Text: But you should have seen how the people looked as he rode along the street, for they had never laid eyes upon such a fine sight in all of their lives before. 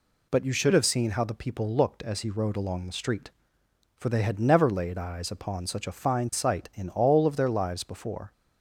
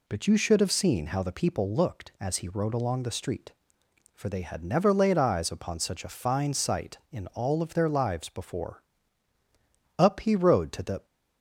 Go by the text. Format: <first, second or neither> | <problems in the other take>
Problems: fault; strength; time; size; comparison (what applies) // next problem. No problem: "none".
first | goes on to say "Up he rode to the"; noticeable; from 9.9 s on; 1.0 s long